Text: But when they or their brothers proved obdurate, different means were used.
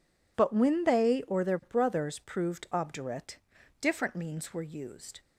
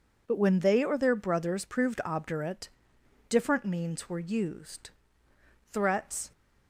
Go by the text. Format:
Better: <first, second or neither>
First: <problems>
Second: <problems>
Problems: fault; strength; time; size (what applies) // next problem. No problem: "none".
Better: first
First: none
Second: goes on to say "Threats"; from 5.7 s on; 0.60 s long